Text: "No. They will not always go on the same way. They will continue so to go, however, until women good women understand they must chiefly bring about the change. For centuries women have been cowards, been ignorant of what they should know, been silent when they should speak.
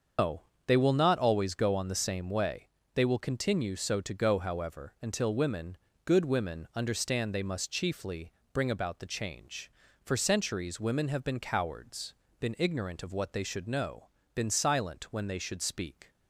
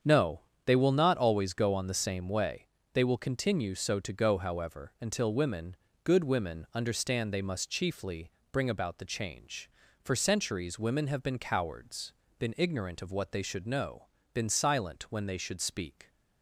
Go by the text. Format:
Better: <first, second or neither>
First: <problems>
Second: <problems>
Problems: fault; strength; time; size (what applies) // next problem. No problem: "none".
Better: second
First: loses the start of "No"; at 0.1 s; 145 ms // starts louder than the rest; until 1.4 s; 7 dB // pauses between "women" and "good"; slight; at 5.7 s; 0.28 s long // pauses between "chiefly" and "bring"; slight; at 8.3 s; 0.20 s long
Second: starts louder than the rest; strong; until 1.2 s; 8 dB // pauses between "women" and "good"; slight; at 5.7 s; 0.28 s long // pauses between "chiefly" and "bring"; slight; at 8.3 s; 0.20 s long